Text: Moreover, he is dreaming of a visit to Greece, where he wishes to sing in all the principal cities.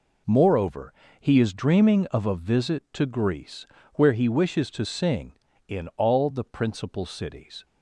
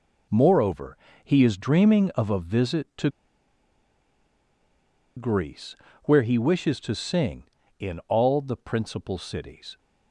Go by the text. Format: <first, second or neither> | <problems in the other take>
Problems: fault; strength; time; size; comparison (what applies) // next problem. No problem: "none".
first | pauses between "to" and "Greece"; strong; at 3.0 s; 2.0 s long